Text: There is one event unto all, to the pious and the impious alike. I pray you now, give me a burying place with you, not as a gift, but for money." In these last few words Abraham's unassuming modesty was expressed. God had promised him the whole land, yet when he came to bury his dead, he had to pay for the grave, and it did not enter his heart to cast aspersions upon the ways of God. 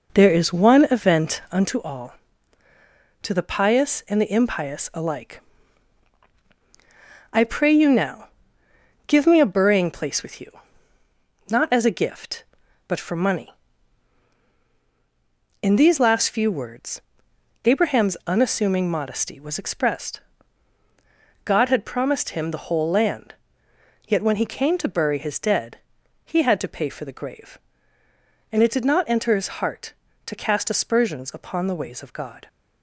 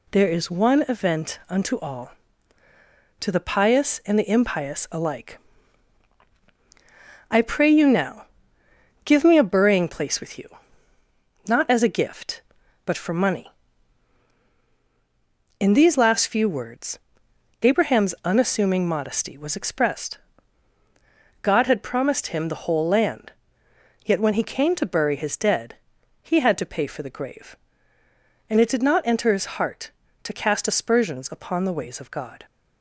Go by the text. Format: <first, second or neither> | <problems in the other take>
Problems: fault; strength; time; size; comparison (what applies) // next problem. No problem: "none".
second | starts louder than the rest; noticeable; until 1.8 s; 5 dB // pauses between "words" and "Abraham's"; noticeable; at 17.0 s; 0.62 s long; noticeable in the second